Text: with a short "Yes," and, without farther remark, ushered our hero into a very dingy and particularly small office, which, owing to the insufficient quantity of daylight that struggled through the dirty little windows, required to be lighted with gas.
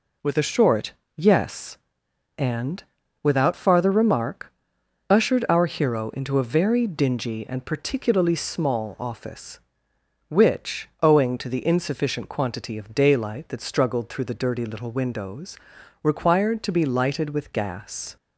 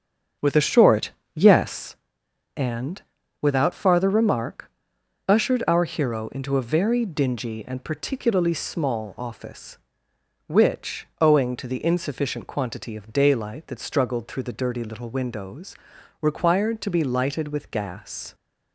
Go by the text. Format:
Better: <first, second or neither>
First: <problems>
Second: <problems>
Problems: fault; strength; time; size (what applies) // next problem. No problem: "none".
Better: first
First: pauses between "short" and "Yes"; slight; at 0.9 s; 0.24 s long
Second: starts louder than the rest; strong; until 1.9 s; 7.5 dB // pauses between "short" and "Yes"; slight; at 1.1 s; 0.24 s long